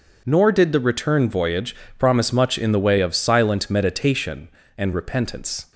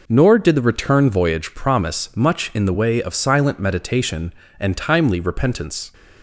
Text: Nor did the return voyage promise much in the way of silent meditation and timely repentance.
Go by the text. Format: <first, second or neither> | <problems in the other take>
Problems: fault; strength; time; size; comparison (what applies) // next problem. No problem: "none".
second | pauses between "voyage" and "promise"; slight; at 1.7 s; 0.22 s long // skips "timely"; at 4.9 s